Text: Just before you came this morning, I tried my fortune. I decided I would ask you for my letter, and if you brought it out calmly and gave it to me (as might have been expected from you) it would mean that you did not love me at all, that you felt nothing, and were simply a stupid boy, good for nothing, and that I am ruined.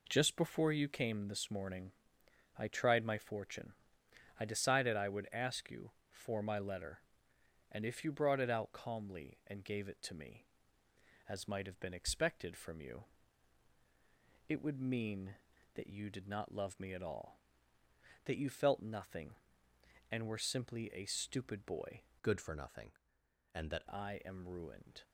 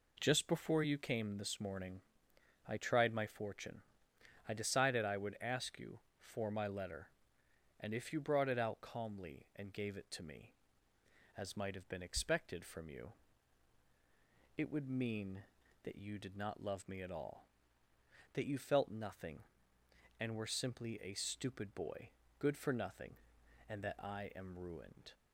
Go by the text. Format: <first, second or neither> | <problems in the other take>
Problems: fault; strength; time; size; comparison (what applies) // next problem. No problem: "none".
second | changes voice from "good" to "that"; from 22.2 to 23.8 s; 1.6 s long